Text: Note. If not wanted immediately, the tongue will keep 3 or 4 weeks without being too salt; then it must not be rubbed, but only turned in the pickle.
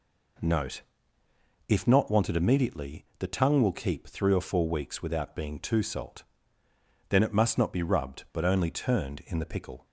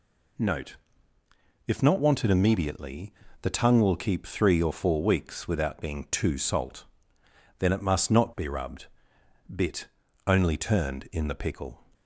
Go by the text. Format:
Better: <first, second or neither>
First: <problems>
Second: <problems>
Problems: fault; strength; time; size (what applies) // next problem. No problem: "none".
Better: first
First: none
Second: says "bit" for "but"; at 9.5 s